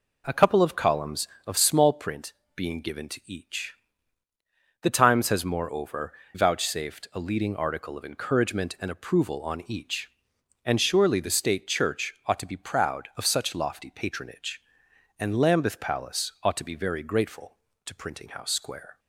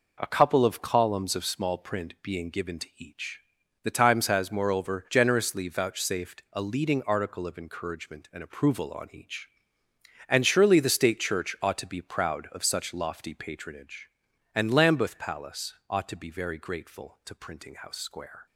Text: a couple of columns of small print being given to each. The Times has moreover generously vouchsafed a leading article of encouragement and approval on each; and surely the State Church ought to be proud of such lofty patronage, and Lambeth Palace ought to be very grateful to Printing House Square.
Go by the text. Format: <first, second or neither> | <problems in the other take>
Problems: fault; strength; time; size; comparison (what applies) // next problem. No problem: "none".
second | pauses between "print" and "being"; slight; at 2.3 s; 0.22 s long // skips "generously"; at 6.2 s